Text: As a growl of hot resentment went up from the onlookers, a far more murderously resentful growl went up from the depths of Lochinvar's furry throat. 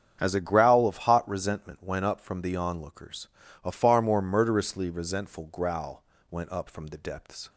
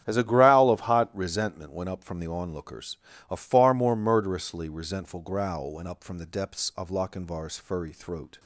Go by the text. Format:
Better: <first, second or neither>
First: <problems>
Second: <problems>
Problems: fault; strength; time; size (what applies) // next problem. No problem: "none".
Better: second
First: starts louder than the rest; strong; until 1.2 s; 8 dB // pauses between "growl" and "went"; slight; at 6.0 s; 0.26 s long // stops before "of Lochinvar's furry throat"; at 7.4 s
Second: starts louder than the rest; strong; until 1.0 s; 9.5 dB